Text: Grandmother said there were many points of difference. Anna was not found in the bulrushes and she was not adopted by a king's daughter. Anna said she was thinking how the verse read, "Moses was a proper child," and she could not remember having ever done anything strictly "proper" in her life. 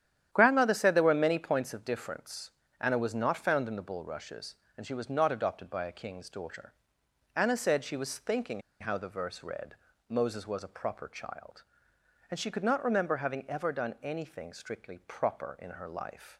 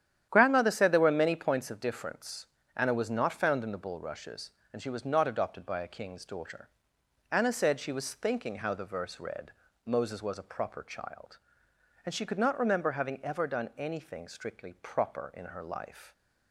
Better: second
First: starts louder than the rest; strong; until 1.3 s; 10.5 dB // pauses between "thinking" and "how"; slight; at 8.6 s; 0.20 s long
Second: starts louder than the rest; strong; until 1.3 s; 10.5 dB

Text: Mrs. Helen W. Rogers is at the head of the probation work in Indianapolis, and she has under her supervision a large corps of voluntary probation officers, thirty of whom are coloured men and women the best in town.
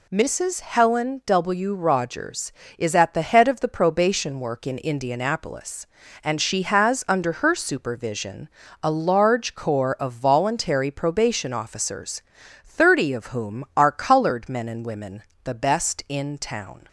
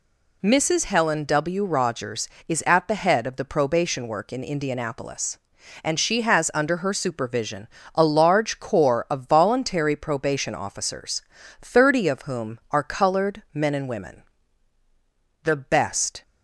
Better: first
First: pauses between "supervision" and "a"; slight; at 8.4 s; 0.34 s long // pauses between "women" and "the"; slight; at 15.2 s; 0.20 s long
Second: pauses between "supervision" and "a"; slight; at 7.6 s; 0.30 s long // pauses between "women" and "the"; at 14.2 s; 1.2 s long // stops before "in town"; at 16.2 s

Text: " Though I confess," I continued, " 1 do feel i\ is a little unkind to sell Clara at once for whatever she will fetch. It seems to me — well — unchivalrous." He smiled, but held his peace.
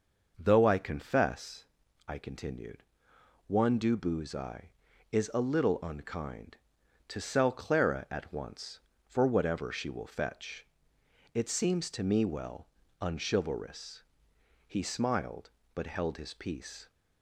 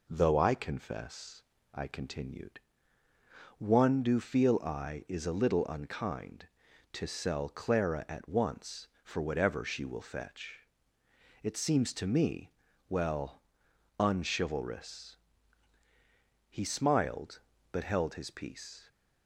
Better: second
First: says "booze" for "feel"; at 3.9 s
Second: none

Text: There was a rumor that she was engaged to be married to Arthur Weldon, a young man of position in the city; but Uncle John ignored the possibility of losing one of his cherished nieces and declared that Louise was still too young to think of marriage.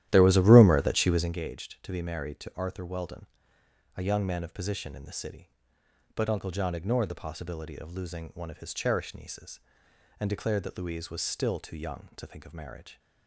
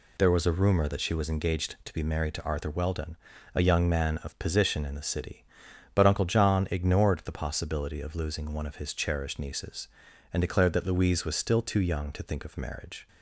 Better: second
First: starts louder than the rest; strong; until 1.4 s; 12.5 dB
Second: none

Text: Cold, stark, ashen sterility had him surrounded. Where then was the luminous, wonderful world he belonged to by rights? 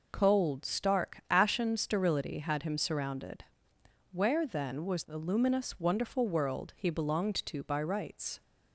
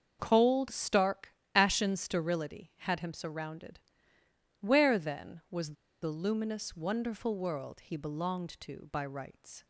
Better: first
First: none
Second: starts louder than the rest; until 1.2 s; 6.5 dB // pauses between "was" and "the"; slight; at 5.7 s; 0.29 s long

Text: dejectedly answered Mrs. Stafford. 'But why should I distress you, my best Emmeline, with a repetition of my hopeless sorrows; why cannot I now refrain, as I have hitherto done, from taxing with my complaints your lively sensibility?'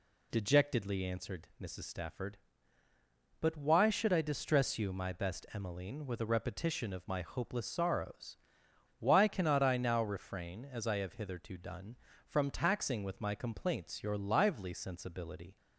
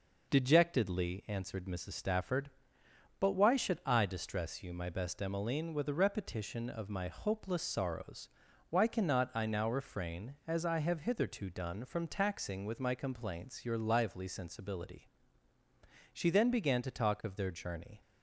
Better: first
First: none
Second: goes on to say "She then began to talk of their journey"; strong; from 16.1 s on; 1.8 s long

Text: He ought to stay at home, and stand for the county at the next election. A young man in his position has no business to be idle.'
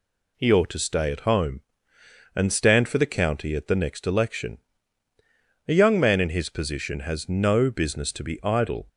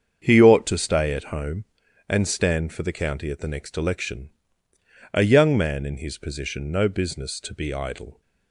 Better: first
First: none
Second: starts louder than the rest; strong; until 1.2 s; 7 dB // skips "has"; at 6.7 s

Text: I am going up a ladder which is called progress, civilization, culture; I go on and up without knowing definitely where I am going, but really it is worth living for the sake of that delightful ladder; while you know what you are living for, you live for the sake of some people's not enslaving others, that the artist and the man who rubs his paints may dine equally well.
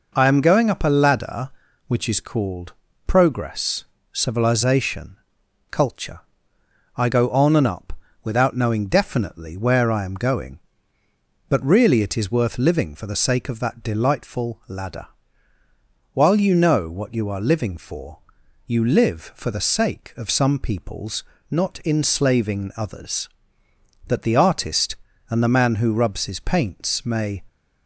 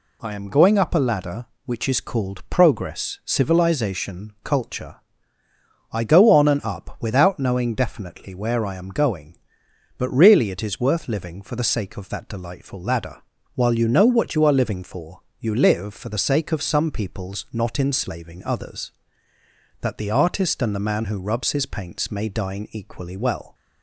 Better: second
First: pauses between "called" and "progress"; slight; at 2.7 s; 0.32 s long // pauses between "up" and "without"; slight; at 7.9 s; 0.28 s long // pauses between "people's" and "not"; slight; at 21.2 s; 0.26 s long // stops before "dine equally well"; at 27.4 s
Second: none

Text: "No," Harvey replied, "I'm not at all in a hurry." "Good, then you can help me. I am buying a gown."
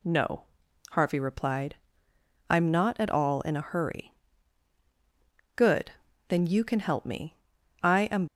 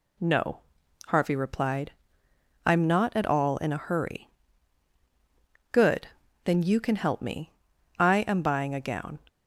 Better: second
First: stops before "buying a gown"; at 8.2 s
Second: none

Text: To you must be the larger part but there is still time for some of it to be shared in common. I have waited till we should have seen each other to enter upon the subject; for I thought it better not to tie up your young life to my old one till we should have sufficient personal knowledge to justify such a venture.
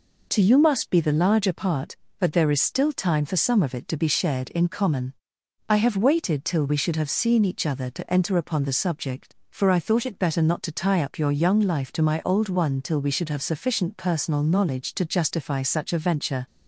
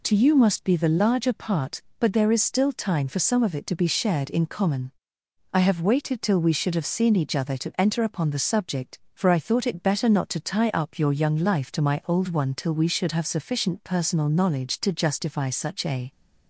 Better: first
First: none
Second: stops before "venture"; at 16.1 s

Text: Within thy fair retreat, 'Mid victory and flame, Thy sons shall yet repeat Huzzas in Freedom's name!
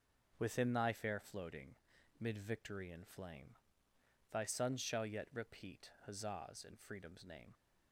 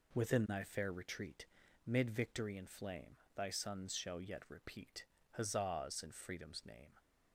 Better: second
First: says "floating" for "retreat"; at 1.1 s // pauses between "repeat" and "Huzzas"; slight; at 5.9 s; 0.16 s long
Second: pauses between "repeat" and "Huzzas"; slight; at 5.0 s; 0.26 s long

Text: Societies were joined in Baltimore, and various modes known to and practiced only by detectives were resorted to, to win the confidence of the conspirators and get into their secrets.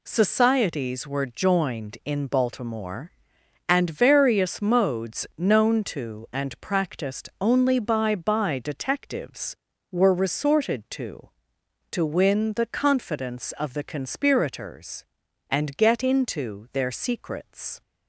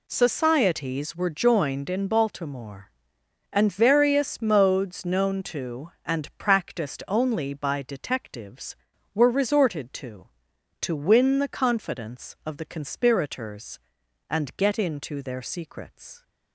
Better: second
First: says "by" twice; at 8.1 s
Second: none

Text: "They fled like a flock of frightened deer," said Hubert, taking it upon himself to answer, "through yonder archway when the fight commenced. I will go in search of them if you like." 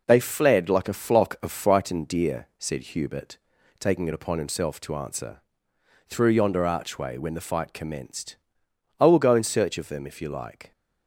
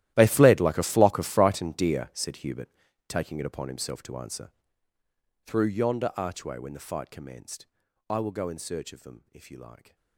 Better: first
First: none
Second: gets quieter; strong; throughout; 18.5 dB

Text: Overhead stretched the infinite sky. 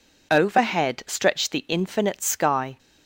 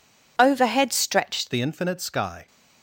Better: first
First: none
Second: changes voice at "the"; from 1.5 s on; 0.9 s long

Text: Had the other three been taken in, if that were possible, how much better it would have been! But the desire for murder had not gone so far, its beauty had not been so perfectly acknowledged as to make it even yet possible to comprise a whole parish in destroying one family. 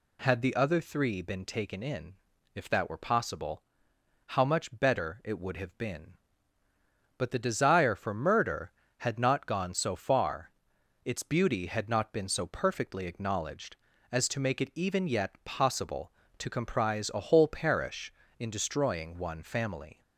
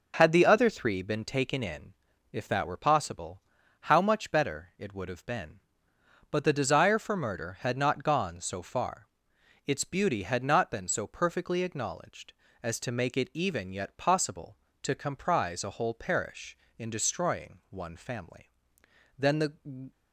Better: first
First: none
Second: goes on to say "Then the"; noticeable; from 19.1 s on; 0.72 s long

